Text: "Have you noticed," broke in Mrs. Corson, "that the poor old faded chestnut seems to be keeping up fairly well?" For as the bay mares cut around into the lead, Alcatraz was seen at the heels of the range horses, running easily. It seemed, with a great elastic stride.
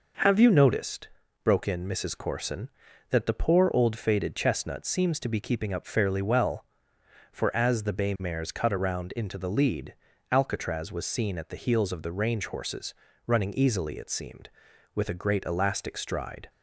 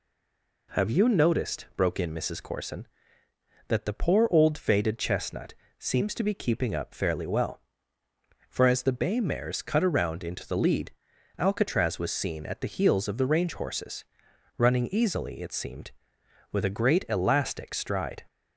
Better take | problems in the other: first | stays silent before the first word; slight; until 0.6 s; 0.6 s long // pauses between "chestnut" and "seems"; slight; at 5.5 s; 0.24 s long

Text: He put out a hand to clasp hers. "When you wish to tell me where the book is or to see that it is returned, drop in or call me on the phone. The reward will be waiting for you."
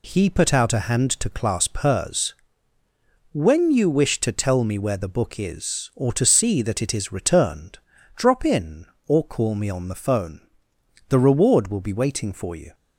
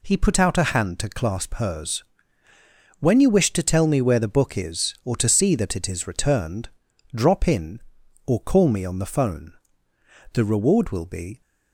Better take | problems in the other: first | stops before "waiting for you"; at 11.4 s

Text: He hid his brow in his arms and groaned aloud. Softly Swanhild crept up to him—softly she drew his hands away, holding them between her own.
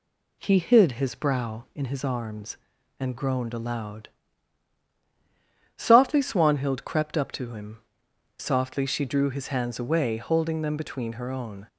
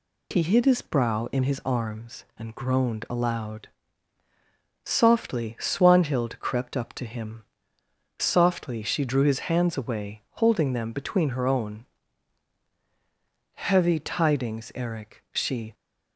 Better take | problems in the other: first | goes on to say "Heavy tidings Eric she"; strong; from 13.5 s on; 2.1 s long

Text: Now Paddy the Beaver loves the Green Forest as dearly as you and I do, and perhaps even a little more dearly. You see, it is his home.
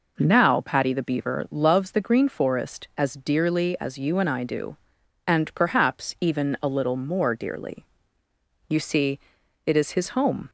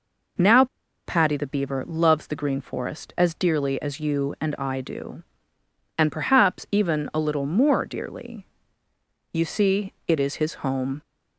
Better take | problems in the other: first | pauses between "Now" and "Paddy"; at 0.6 s; 0.40 s long

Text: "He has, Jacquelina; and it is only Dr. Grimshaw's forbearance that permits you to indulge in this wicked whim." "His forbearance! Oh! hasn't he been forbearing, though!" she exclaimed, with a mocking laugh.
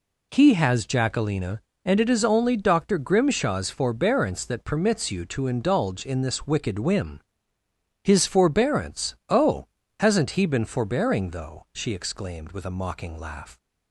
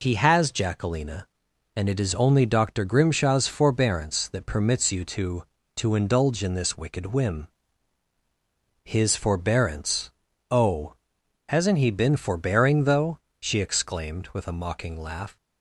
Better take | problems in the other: first | says "to" twice; at 5.7 s

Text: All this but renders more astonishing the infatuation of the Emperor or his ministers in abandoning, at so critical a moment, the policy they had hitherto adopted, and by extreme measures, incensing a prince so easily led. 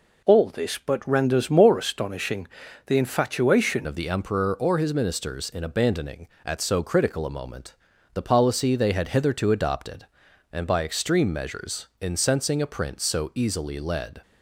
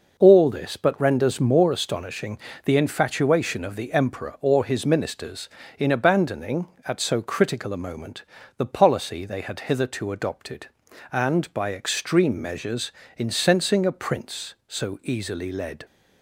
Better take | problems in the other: second | pauses between "astonishing" and "the"; at 2.4 s; 0.38 s long; slight in the second // changes voice at "of"; from 3.8 s on; 10.4 s long

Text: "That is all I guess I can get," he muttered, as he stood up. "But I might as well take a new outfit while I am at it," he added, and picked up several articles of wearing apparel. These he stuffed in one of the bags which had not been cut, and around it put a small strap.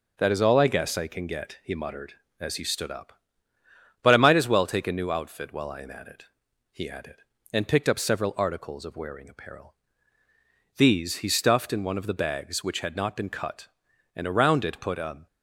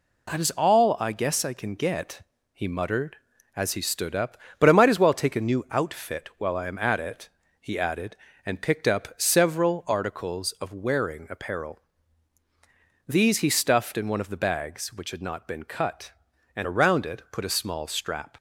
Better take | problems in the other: second | stops before "small strap"; at 15.2 s

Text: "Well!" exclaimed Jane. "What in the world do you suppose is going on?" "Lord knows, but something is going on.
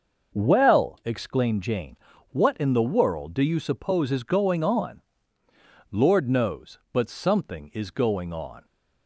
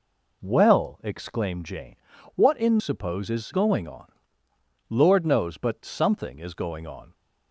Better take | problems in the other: first | skips "the world do you"; at 2.7 s

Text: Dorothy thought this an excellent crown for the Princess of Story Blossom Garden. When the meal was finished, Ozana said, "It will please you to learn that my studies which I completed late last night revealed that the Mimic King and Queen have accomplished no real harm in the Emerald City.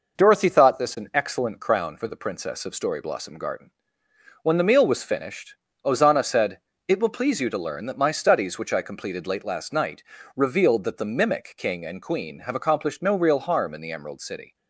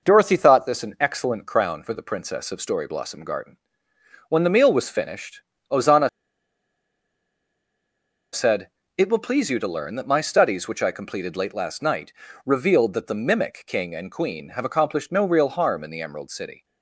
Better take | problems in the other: first | pauses between "Ozana" and "said"; strong; at 6.0 s; 2.2 s long // pauses between "night" and "revealed"; slight; at 12.1 s; 0.34 s long; slight in the first

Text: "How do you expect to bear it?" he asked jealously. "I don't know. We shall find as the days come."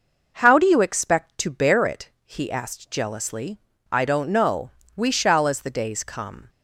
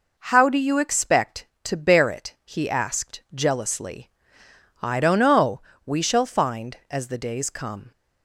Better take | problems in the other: second | skips "find"; at 5.4 s

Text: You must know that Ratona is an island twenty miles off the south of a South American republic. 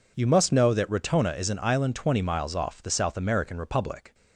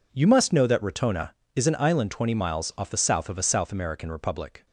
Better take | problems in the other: second | skips "south of a"; at 2.9 s

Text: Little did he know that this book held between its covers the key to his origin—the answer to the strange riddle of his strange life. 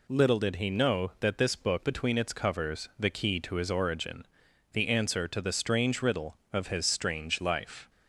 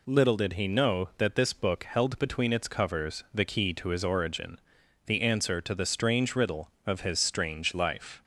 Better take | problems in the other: second | skips "held"; at 1.8 s

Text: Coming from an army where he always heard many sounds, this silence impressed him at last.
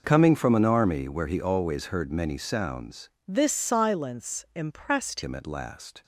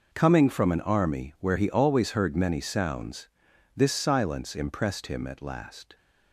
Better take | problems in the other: second | changes voice from "this" to "impressed"; from 3.2 to 5.2 s; 2.0 s long

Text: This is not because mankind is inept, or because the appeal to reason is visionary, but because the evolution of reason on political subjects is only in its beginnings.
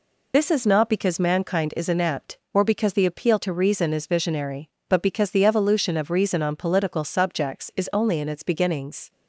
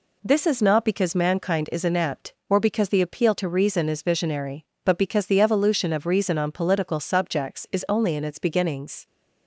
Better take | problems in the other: second | loses the start of "This"; at 0.3 s; 85 ms

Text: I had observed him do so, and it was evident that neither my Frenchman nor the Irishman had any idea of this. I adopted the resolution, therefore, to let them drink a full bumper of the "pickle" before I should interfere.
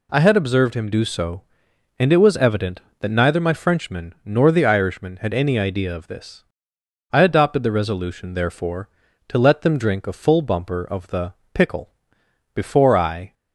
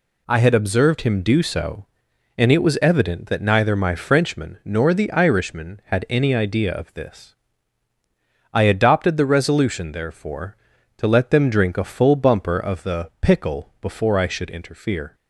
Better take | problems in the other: second | pauses between "the" and "pickle"; slight; at 11.3 s; 0.20 s long // pauses between "pickle" and "before"; noticeable; at 11.9 s; 0.62 s long // stops before "should interfere"; at 13.3 s

